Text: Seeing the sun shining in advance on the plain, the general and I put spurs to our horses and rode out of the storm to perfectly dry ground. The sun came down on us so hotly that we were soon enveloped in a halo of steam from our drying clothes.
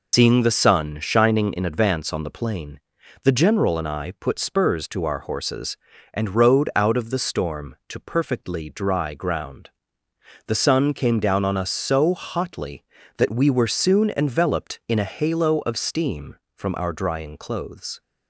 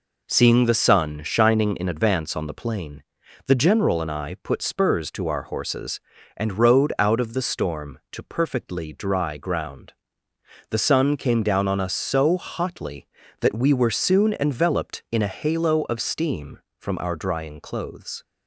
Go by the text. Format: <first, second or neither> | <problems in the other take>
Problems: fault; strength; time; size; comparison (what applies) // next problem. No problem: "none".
second | loses the start of "Seeing"; at 0.1 s; 90 ms